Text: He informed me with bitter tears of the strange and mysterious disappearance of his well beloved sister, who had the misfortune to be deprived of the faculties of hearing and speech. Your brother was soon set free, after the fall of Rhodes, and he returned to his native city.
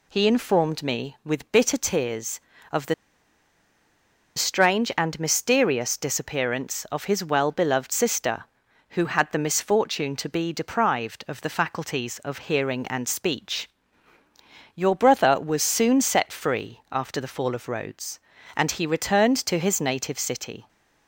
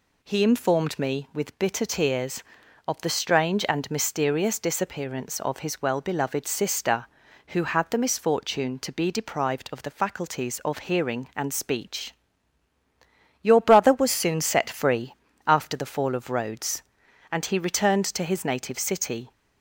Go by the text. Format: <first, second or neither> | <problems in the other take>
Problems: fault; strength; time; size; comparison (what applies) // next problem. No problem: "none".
second | pauses between "the" and "strange"; strong; at 2.9 s; 1.4 s long